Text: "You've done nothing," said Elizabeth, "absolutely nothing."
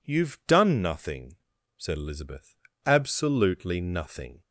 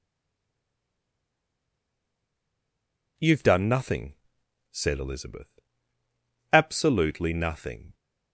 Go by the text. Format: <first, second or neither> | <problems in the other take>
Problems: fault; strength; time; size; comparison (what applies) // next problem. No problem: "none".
first | stays silent before the first word; strong; until 3.1 s; 3.1 s long